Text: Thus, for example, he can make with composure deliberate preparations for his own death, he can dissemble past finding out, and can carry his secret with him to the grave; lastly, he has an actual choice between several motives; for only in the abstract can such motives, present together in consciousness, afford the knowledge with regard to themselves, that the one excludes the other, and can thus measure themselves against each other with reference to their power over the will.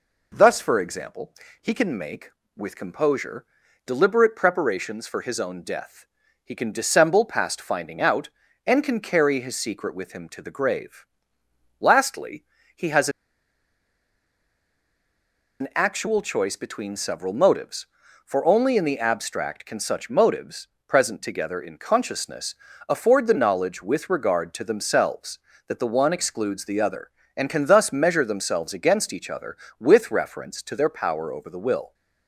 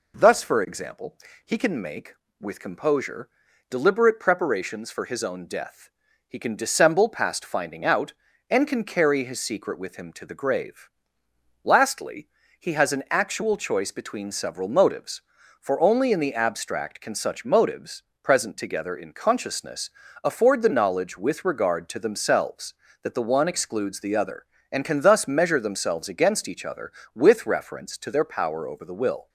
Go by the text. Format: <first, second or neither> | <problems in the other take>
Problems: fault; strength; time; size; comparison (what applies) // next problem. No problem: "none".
second | pauses between "composure" and "deliberate"; at 3.4 s; 0.40 s long; also in the second // pauses between "has" and "an"; strong; at 13.0 s; 2.5 s long